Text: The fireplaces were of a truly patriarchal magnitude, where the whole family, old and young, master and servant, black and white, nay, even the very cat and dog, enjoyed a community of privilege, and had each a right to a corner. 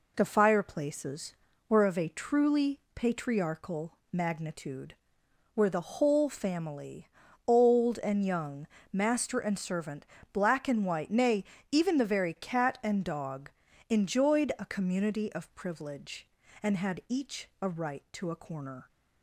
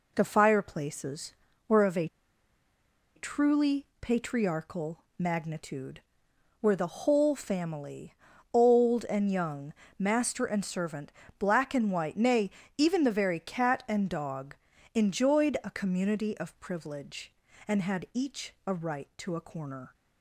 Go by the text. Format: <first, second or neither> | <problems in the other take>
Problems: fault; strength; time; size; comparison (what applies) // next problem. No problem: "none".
first | pauses between "a" and "truly"; at 2.0 s; 1.0 s long // pauses between "truly" and "patriarchal"; slight; at 3.8 s; 0.16 s long; slight in the first // pauses between "patriarchal" and "magnitude"; slight; at 5.0 s; 0.16 s long; slight in the first